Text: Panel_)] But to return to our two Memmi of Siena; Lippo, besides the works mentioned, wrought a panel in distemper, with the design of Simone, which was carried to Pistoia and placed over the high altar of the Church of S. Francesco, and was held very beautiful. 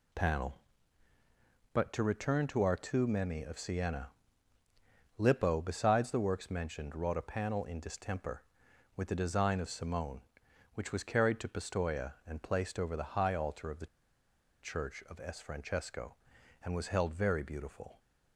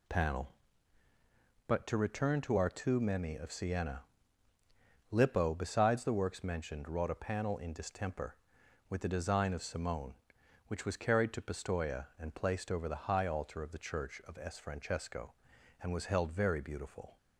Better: second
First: pauses between "the" and "Church"; noticeable; at 13.8 s; 0.76 s long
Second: none

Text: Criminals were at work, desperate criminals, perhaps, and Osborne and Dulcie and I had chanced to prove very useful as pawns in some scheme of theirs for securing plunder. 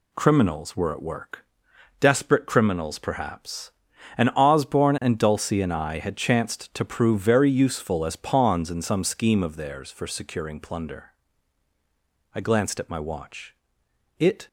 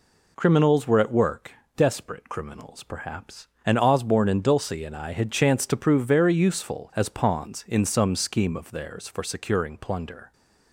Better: second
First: goes on to say "I glanced at my watch It"; strong; from 12.3 s on; 2.1 s long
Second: none

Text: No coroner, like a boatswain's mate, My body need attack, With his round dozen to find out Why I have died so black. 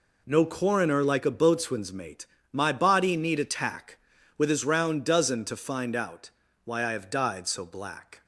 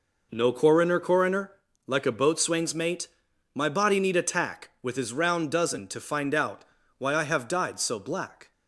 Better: first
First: pauses between "out" and "Why"; slight; at 6.2 s; 0.34 s long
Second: says "coroner" twice; at 0.9 s // pauses between "out" and "Why"; slight; at 6.6 s; 0.34 s long

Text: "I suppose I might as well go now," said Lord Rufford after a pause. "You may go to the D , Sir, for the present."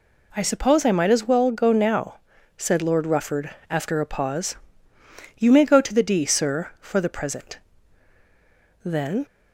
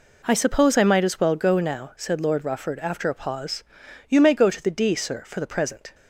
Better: second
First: pauses between "Rufford" and "after"; slight; at 3.4 s; 0.20 s long // goes on to say "Then"; slight; from 8.8 s on; 0.40 s long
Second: none

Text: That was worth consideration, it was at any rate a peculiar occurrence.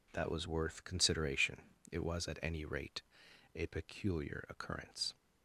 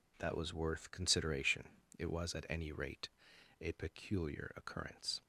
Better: neither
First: pauses between "rate" and "a"; noticeable; at 3.0 s; 0.52 s long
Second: pauses between "rate" and "a"; noticeable; at 3.0 s; 0.50 s long

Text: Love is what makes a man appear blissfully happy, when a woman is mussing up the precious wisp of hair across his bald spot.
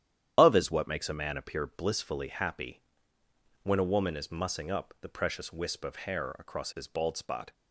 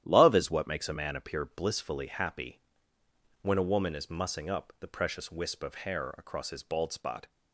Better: second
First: loses the start of "Love"; at 0.3 s; 125 ms // starts louder than the rest; strong; until 1.3 s; 10 dB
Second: starts louder than the rest; strong; until 1.0 s; 11.5 dB

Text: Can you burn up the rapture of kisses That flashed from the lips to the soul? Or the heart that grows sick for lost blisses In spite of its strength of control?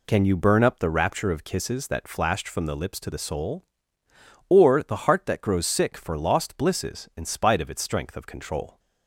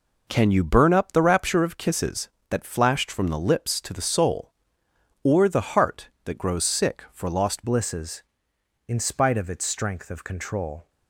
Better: first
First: none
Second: changes voice at "blisses"; from 7.6 s on; 3.2 s long

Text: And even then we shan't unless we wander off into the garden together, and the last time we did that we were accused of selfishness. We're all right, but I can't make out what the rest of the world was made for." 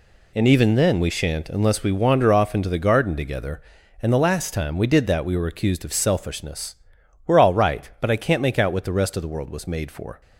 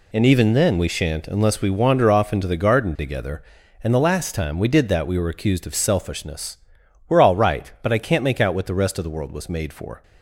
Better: neither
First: none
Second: none

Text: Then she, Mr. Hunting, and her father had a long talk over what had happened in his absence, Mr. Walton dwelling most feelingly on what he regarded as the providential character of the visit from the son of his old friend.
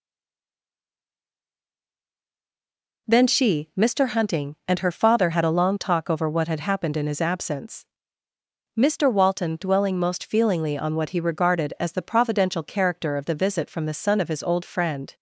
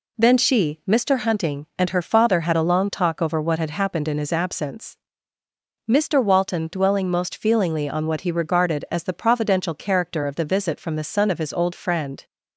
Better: second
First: stays silent before the first word; strong; until 3.0 s; 3.0 s long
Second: none

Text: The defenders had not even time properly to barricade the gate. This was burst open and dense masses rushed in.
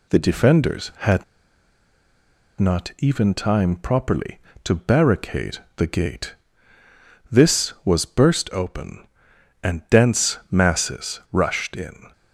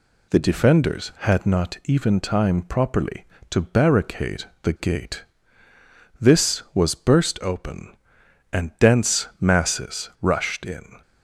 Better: second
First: pauses between "had" and "not"; strong; at 1.2 s; 1.3 s long // pauses between "barricade" and "the"; slight; at 5.5 s; 0.18 s long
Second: pauses between "barricade" and "the"; slight; at 4.4 s; 0.18 s long

